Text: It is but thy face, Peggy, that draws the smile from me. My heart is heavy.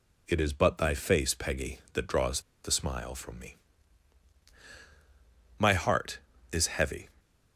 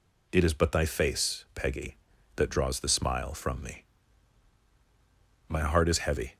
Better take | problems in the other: second | pauses between "draws" and "the"; slight; at 2.4 s; 0.23 s long

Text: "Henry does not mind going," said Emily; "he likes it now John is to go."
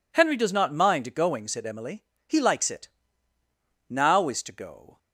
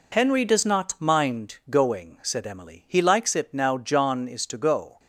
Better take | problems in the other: second | pauses between "it" and "now"; noticeable; at 2.8 s; 0.98 s long // skips "John"; at 4.2 s

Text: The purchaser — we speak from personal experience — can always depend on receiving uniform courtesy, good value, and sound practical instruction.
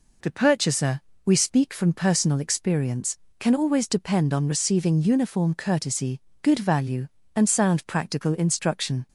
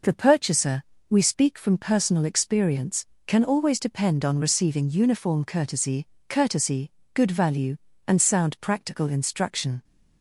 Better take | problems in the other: first | says "courtesy" twice; at 6.2 s

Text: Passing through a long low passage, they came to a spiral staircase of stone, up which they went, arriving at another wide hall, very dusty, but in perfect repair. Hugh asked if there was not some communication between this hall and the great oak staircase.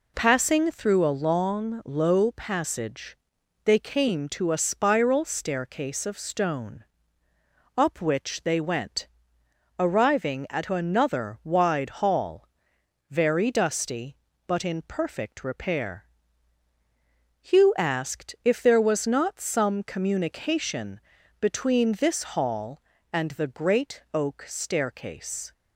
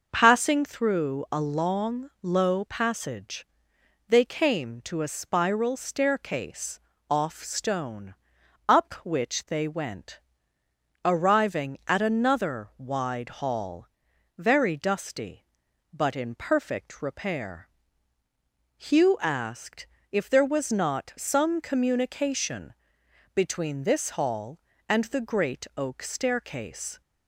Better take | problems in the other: first | says "off" for "of"; at 7.1 s // pauses between "asked" and "if"; slight; at 19.8 s; 0.26 s long // pauses between "communication" and "between"; noticeable; at 22.7 s; 0.60 s long; also in the first

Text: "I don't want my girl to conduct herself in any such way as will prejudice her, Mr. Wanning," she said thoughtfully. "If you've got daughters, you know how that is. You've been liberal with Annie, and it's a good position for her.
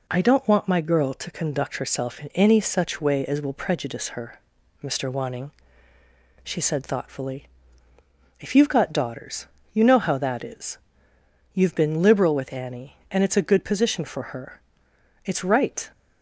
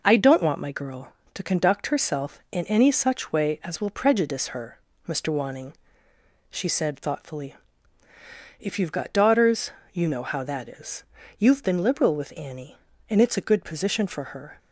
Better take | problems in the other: second | goes on to say "It's right"; noticeable; from 15.2 s on; 0.66 s long

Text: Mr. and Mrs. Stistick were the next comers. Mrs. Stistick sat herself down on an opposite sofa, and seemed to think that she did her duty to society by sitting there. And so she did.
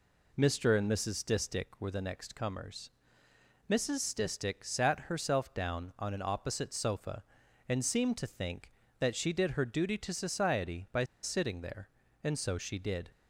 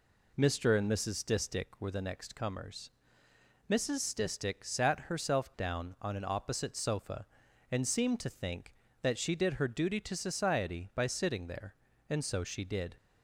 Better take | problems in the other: second | pauses between "by" and "sitting"; slight; at 11.0 s; 0.19 s long

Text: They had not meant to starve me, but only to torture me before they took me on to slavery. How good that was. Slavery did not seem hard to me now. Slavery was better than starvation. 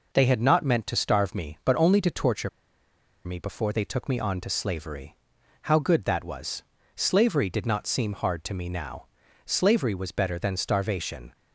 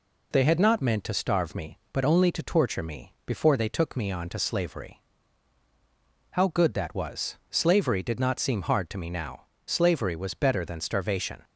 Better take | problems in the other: second | pauses between "torture" and "me"; noticeable; at 2.4 s; 0.76 s long

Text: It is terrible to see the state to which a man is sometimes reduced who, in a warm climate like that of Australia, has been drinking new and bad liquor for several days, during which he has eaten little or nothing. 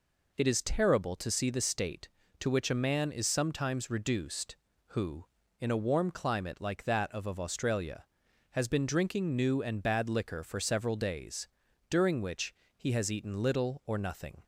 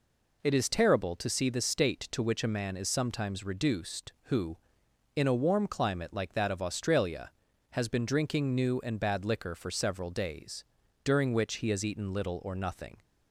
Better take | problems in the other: second | says "of" twice; at 7.2 s // pauses between "which" and "he"; slight; at 12.5 s; 0.26 s long

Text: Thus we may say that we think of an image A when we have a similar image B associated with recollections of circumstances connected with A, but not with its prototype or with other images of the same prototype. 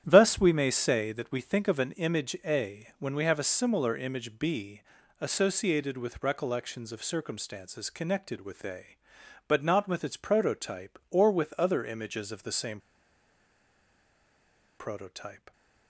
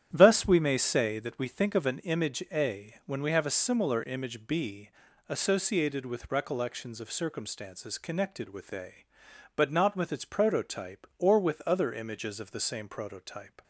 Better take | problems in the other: second | starts louder than the rest; strong; until 1.0 s; 10 dB; strong in the second // pauses between "B" and "associated"; at 4.8 s; 0.38 s long; also in the second // pauses between "same" and "prototype"; strong; at 12.7 s; 1.9 s long

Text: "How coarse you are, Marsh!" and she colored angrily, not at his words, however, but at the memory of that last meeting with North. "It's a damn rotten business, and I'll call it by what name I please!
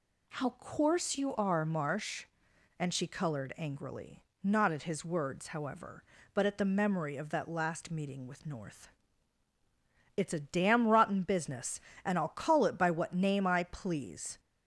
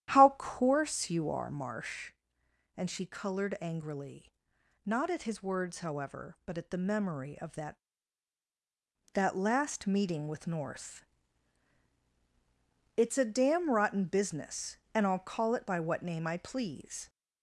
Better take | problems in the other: first | starts louder than the rest; strong; until 1.2 s; 11.5 dB // says "that" twice; at 9.1 s

